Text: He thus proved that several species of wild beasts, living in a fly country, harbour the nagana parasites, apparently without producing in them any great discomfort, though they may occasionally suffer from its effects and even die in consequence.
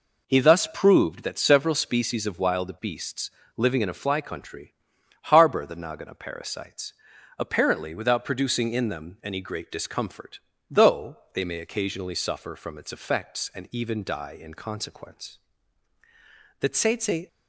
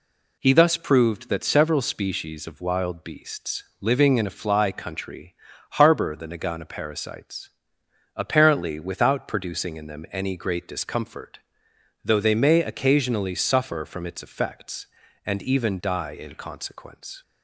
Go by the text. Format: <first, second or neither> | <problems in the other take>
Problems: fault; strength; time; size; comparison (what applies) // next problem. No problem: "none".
second | pauses between "though" and "they"; slight; at 11.1 s; 0.18 s long // goes on to say "The tsetse"; noticeable; from 16.5 s on; 0.68 s long